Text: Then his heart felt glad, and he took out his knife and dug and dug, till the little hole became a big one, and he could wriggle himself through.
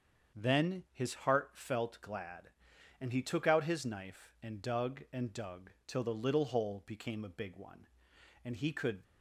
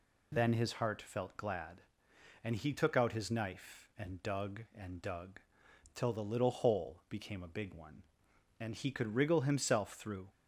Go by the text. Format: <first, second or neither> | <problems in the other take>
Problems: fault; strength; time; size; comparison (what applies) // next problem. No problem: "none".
second | starts louder than the rest; strong; until 1.4 s; 7 dB // stops before "wriggle himself through"; at 9.0 s